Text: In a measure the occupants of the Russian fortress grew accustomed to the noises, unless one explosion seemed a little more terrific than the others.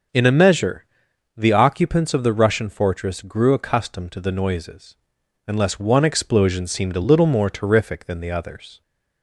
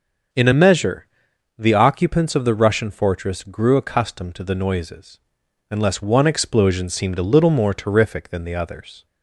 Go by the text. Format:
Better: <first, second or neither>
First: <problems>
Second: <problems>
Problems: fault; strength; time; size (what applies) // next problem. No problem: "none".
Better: neither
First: starts louder than the rest; noticeable; until 1.6 s; 6 dB // pauses between "measure" and "the"; noticeable; at 0.8 s; 0.52 s long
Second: starts louder than the rest; until 1.8 s; 6.5 dB // pauses between "measure" and "the"; noticeable; at 1.0 s; 0.52 s long